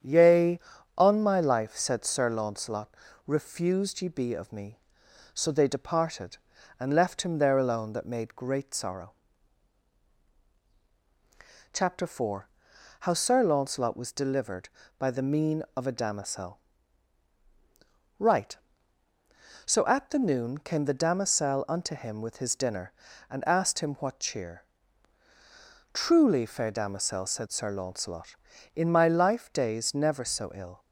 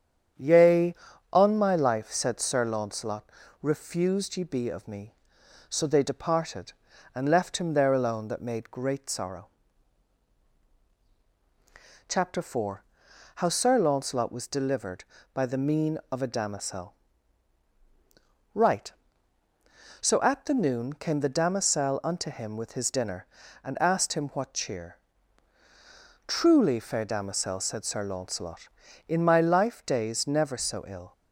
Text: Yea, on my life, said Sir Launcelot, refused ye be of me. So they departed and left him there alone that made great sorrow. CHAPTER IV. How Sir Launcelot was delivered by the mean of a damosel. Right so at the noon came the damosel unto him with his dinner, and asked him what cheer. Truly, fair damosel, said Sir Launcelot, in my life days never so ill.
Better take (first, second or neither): neither